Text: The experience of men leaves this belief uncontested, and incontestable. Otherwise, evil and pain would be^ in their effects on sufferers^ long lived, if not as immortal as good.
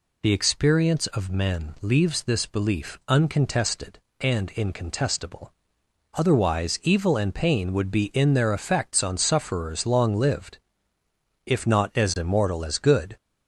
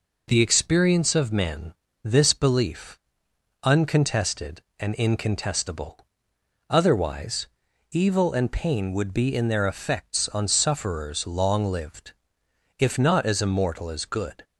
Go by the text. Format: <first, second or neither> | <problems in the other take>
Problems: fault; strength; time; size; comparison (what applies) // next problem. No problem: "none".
first | skips "leaves"; at 1.8 s // pauses between "belief" and "uncontested"; noticeable; at 2.9 s; 0.66 s long